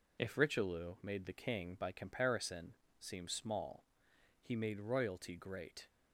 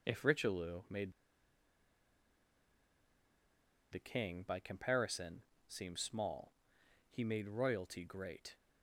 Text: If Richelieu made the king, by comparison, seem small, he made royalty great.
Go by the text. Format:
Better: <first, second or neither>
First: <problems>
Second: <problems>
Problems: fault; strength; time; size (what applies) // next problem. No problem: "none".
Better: first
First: none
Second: pauses between "made" and "the"; strong; at 1.1 s; 2.7 s long